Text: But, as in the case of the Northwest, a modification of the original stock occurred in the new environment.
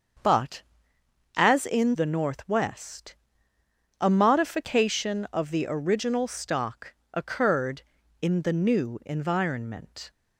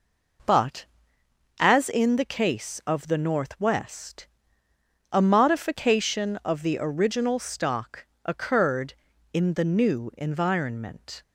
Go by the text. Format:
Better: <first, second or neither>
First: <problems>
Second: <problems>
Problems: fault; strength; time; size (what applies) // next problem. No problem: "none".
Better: second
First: starts louder than the rest; until 1.9 s; 7 dB // skips "the case of"; at 1.9 s // pauses between "stock" and "occurred"; slight; at 6.9 s; 0.18 s long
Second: pauses between "stock" and "occurred"; slight; at 8.0 s; 0.18 s long